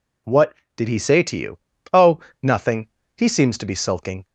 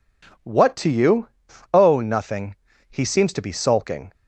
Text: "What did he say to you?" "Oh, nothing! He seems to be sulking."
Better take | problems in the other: first | skips "did he say"; at 0.7 s

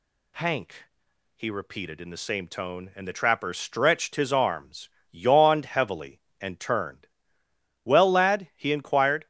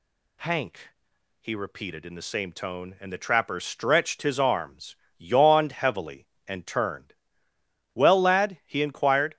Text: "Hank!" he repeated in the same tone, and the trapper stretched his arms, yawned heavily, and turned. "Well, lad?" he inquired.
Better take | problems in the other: neither | none

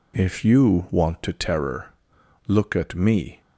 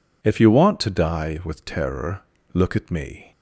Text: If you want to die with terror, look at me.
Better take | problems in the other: second | skips "die with"; at 1.3 s

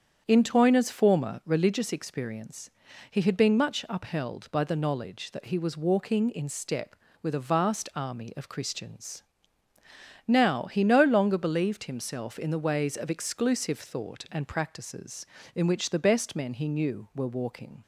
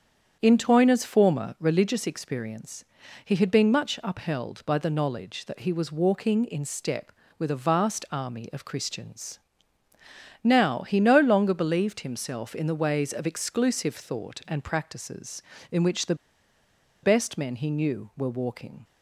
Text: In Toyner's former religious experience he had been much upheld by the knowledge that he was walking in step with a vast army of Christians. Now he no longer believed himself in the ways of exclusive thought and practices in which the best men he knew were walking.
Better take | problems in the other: first | starts louder than the rest; strong; until 1.4 s; 8 dB; strong in the first // pauses between "experience" and "he"; at 2.8 s; 0.40 s long; also in the first // pauses between "the" and "best"; noticeable; at 16.1 s; 0.88 s long

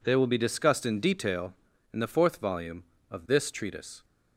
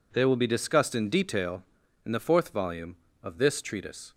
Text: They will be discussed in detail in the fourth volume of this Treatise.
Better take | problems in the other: neither | none

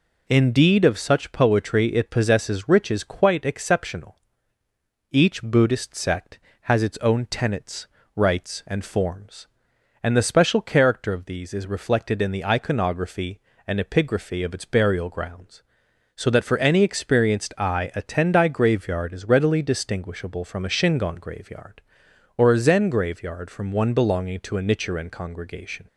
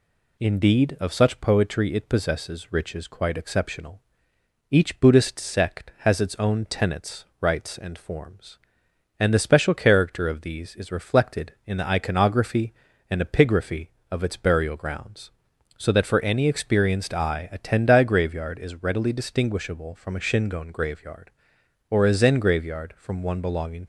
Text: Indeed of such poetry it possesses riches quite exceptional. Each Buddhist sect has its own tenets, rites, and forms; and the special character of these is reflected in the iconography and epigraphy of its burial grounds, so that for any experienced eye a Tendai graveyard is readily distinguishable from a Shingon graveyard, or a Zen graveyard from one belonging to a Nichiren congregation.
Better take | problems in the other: first | stops before "to a Nichiren congregation"; at 23.8 s

